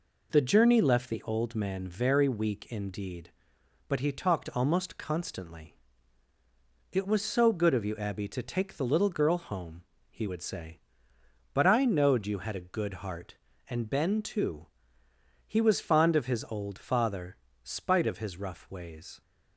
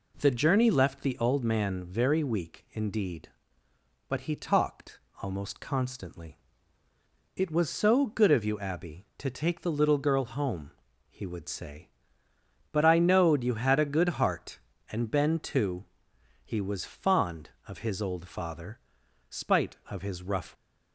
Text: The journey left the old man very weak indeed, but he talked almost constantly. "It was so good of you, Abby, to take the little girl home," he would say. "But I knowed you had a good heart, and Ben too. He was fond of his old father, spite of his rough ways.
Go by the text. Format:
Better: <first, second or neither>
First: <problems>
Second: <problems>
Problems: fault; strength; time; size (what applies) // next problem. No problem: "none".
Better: first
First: none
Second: pauses between "talked" and "almost"; slight; at 4.9 s; 0.24 s long // stops before "ways"; at 20.5 s